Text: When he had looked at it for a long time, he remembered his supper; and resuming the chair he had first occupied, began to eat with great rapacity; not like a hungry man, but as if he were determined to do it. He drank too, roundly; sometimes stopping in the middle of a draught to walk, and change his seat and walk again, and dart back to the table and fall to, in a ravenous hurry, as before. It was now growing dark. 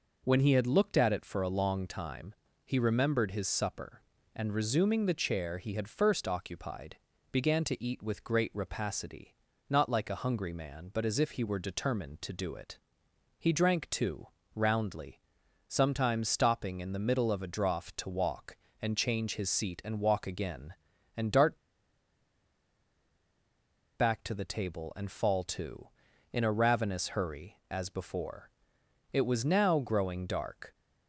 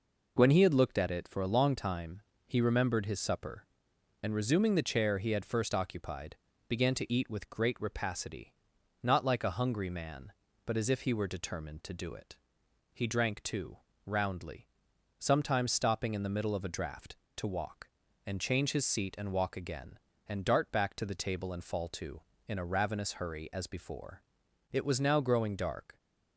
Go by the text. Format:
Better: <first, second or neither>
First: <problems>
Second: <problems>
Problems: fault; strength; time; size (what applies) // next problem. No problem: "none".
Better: second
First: pauses between "dart" and "back"; strong; at 21.5 s; 2.4 s long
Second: none